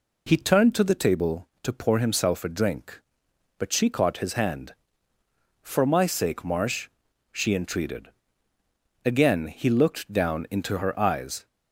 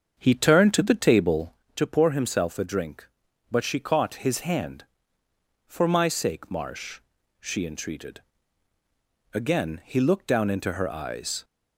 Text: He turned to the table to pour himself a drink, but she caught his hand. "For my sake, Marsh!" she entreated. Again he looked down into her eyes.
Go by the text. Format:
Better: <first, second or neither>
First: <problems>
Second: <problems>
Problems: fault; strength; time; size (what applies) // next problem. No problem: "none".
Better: first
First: none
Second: starts louder than the rest; strong; until 1.7 s; 7 dB